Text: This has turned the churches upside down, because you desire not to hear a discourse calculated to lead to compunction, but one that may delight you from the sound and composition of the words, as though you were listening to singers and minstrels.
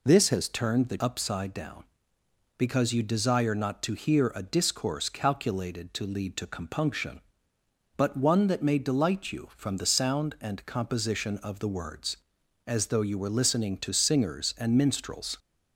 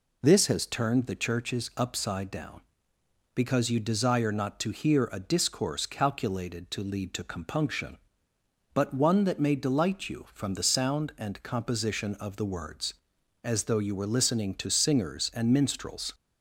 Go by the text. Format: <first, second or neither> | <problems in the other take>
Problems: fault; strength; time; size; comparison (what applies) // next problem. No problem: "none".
second | skips "churches"; at 0.9 s